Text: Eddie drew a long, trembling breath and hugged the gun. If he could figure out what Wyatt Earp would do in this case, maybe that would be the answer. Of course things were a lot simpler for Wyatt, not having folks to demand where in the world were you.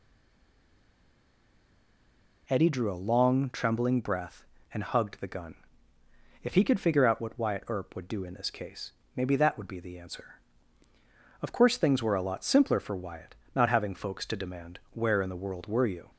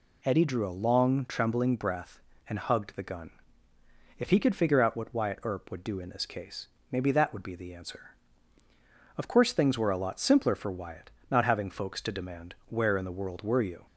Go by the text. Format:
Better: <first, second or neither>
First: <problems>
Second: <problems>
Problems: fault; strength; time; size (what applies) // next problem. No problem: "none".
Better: second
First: stays silent before the first word; until 2.4 s; 2.4 s long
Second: none